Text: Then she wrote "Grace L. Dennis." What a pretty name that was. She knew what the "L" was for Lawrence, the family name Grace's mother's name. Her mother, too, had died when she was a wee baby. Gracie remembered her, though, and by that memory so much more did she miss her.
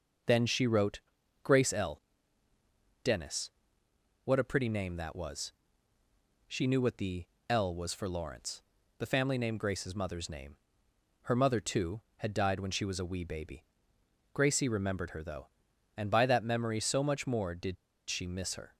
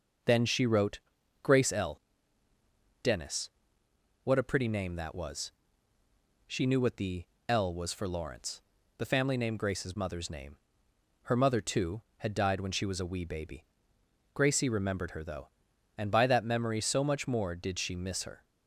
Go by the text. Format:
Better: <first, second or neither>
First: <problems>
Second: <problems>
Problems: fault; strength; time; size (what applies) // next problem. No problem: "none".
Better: second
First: pauses between "wrote" and "Grace"; at 0.9 s; 0.44 s long // pauses between "the" and "L"; slight; at 7.2 s; 0.24 s long // pauses between "did" and "she"; slight; at 17.7 s; 0.33 s long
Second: pauses between "wrote" and "Grace"; at 0.9 s; 0.44 s long // pauses between "the" and "L"; slight; at 7.2 s; 0.24 s long